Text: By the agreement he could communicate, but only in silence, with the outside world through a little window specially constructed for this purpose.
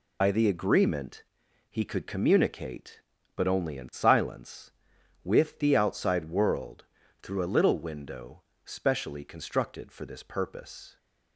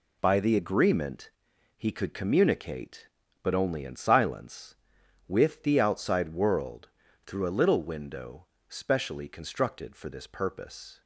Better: second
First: loses the start of "By"; at 0.2 s; 80 ms // pauses between "agreement" and "he"; noticeable; at 1.2 s; 0.48 s long // pauses between "world" and "through"; at 6.8 s; 0.38 s long // pauses between "window" and "specially"; slight; at 8.4 s; 0.22 s long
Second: pauses between "agreement" and "he"; noticeable; at 1.2 s; 0.48 s long // pauses between "world" and "through"; at 6.8 s; 0.38 s long // pauses between "window" and "specially"; slight; at 8.4 s; 0.22 s long

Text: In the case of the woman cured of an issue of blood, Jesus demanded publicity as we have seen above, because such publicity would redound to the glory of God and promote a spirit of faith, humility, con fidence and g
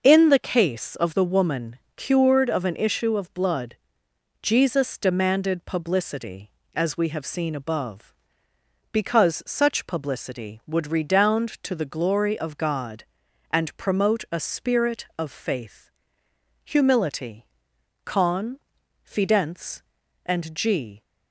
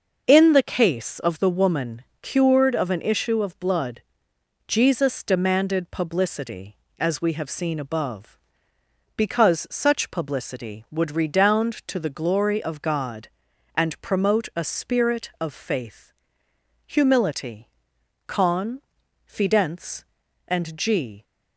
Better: neither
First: pauses between "woman" and "cured"; slight; at 1.7 s; 0.18 s long // pauses between "con" and "fidence"; at 18.5 s; 0.44 s long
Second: pauses between "woman" and "cured"; slight; at 2.0 s; 0.18 s long // pauses between "con" and "fidence"; at 18.8 s; 0.44 s long

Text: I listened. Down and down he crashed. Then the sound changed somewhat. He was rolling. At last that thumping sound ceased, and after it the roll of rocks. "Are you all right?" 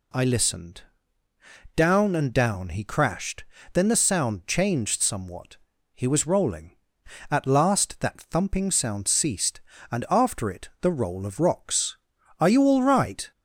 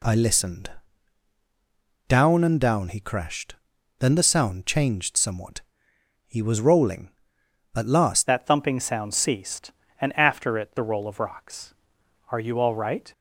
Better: first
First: none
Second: changes voice at "that"; from 8.2 s on; 4.9 s long

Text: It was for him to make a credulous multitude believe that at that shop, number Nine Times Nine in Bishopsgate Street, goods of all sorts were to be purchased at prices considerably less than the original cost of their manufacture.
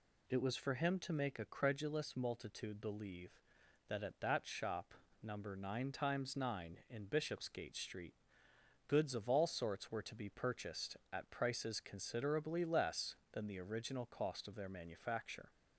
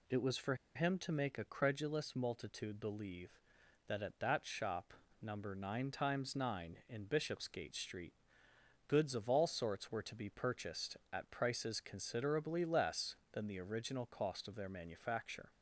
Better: first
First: none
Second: pauses between "for" and "him"; slight; at 0.5 s; 0.21 s long

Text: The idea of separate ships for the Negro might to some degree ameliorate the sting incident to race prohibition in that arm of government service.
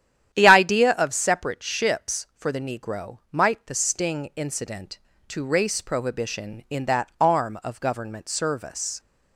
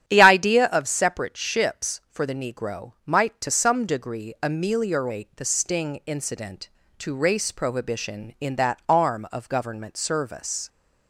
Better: second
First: starts louder than the rest; strong; until 1.3 s; 10.5 dB // skips "to some degree ameliorate"; at 3.6 s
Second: starts louder than the rest; strong; until 1.0 s; 11 dB

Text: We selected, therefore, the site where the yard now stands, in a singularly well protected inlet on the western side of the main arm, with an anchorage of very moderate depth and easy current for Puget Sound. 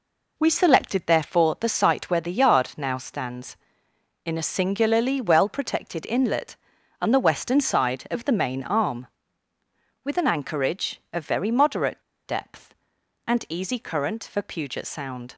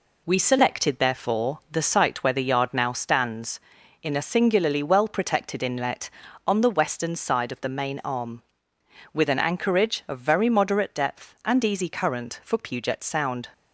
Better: second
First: pauses between "moderate" and "depth"; slight; at 12.0 s; 0.24 s long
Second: none

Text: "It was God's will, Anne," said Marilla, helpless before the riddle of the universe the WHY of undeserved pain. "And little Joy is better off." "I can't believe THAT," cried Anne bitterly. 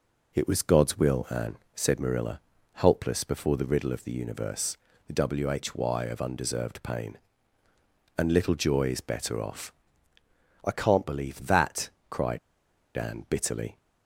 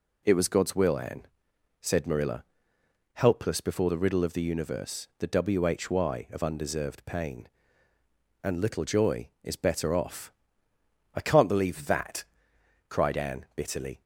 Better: second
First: pauses between "universe" and "the"; slight; at 4.7 s; 0.30 s long // pauses between "cried" and "Anne"; noticeable; at 12.3 s; 0.58 s long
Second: none

